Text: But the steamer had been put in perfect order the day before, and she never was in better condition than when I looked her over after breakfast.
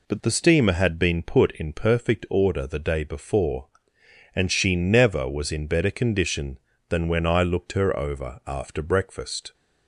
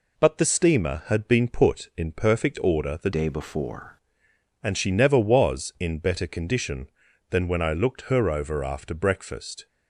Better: first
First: none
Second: changes voice from "day" to "before"; from 3.1 to 3.9 s; 0.8 s long

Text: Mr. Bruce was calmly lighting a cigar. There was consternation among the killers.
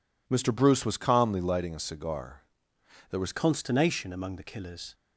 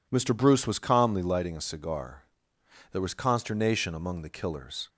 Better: second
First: changes voice at "consternation"; from 3.3 s on; 1.6 s long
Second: none

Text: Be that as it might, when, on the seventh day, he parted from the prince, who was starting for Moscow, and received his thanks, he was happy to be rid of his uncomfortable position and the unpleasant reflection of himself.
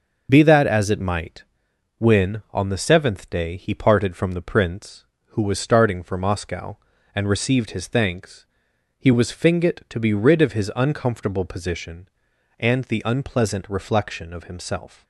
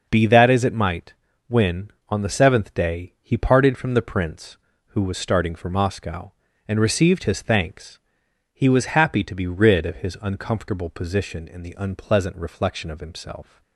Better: second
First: starts louder than the rest; noticeable; until 1.3 s; 6 dB // says "fingit" for "happy"; at 9.3 s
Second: none

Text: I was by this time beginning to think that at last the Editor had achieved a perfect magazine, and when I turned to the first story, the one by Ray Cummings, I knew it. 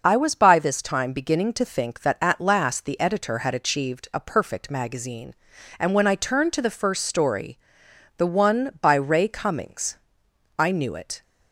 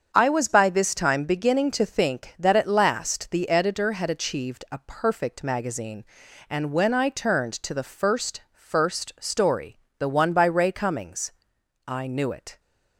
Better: first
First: none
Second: starts louder than the rest; strong; until 1.1 s; 7 dB // says "first" twice; at 8.5 s

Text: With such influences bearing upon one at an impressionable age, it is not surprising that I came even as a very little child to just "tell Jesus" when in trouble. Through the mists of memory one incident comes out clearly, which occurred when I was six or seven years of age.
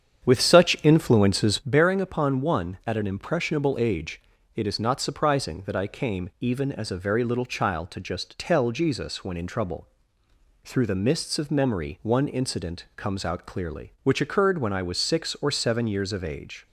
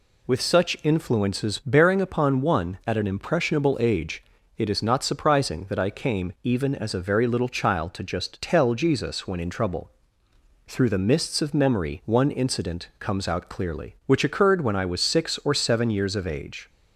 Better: second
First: starts louder than the rest; strong; until 1.7 s; 8.5 dB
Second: none

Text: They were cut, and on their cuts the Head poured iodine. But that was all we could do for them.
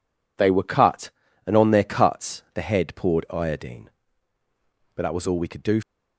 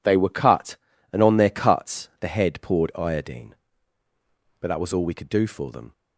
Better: second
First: stops before "for them"; at 5.8 s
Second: none

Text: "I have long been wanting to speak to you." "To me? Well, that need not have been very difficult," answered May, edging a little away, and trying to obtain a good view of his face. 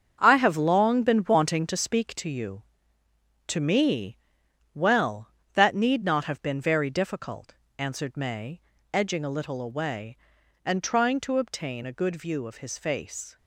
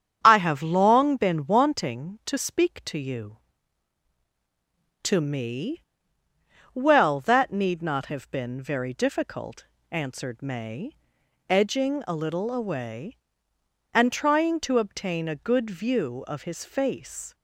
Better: second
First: gets quieter; strong; throughout; 9.5 dB // starts louder than the rest; until 1.2 s; 7 dB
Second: starts louder than the rest; strong; until 1.2 s; 8 dB

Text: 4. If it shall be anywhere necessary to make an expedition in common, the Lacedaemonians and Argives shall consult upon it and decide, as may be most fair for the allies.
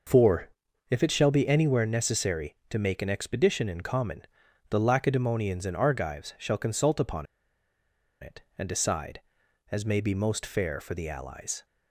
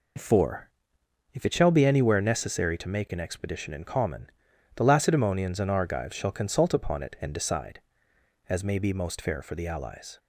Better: second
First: pauses between "upon" and "it"; noticeable; at 7.2 s; 0.95 s long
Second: none

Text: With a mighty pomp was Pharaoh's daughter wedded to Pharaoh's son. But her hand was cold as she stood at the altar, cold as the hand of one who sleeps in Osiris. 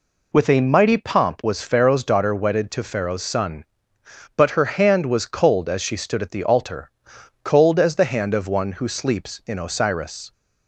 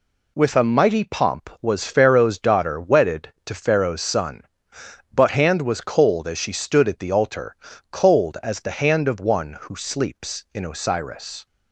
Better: first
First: none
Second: skips "her"; at 5.2 s

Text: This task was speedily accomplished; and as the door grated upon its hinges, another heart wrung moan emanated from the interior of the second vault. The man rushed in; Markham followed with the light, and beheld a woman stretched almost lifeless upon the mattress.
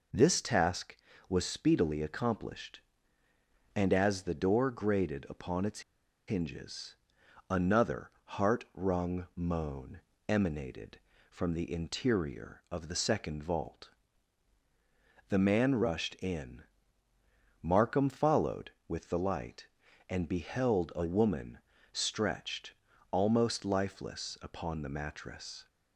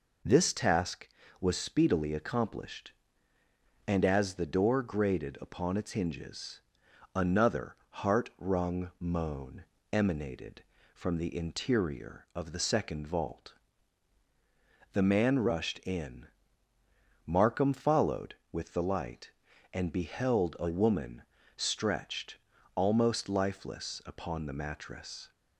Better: second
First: pauses between "its" and "hinges"; noticeable; at 5.8 s; 0.47 s long // pauses between "moan" and "emanated"; slight; at 10.0 s; 0.26 s long // pauses between "woman" and "stretched"; slight; at 21.5 s; 0.34 s long // pauses between "stretched" and "almost"; at 22.7 s; 0.38 s long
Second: pauses between "moan" and "emanated"; slight; at 9.6 s; 0.26 s long // pauses between "woman" and "stretched"; slight; at 21.2 s; 0.34 s long // pauses between "stretched" and "almost"; at 22.3 s; 0.38 s long

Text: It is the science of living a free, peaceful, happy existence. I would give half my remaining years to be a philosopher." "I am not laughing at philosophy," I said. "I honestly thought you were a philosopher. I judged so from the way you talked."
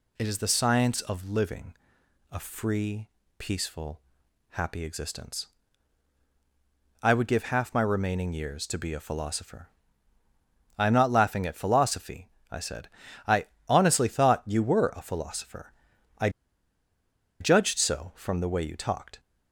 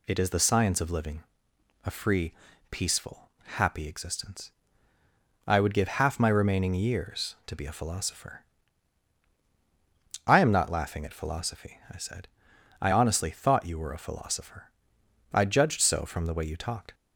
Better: second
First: pauses between "living" and "a"; noticeable; at 1.7 s; 0.56 s long // pauses between "I" and "honestly"; slight; at 13.4 s; 0.20 s long // pauses between "I" and "judged"; at 16.2 s; 1.1 s long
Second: pauses between "living" and "a"; noticeable; at 1.2 s; 0.64 s long

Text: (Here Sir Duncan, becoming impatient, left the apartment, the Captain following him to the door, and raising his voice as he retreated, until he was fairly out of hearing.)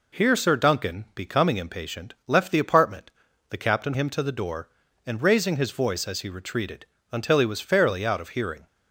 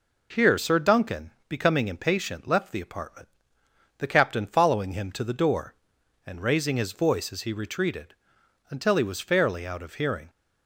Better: second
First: skips "following"; at 3.9 s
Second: none

